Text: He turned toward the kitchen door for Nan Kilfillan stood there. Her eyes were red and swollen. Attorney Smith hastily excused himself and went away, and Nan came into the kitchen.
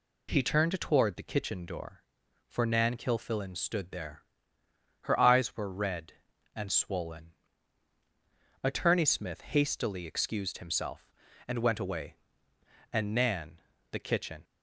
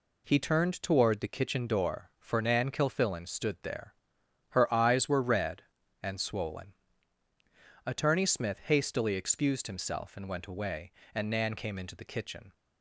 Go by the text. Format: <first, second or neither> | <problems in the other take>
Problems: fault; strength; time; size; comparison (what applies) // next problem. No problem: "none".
second | skips "came into"; at 13.7 s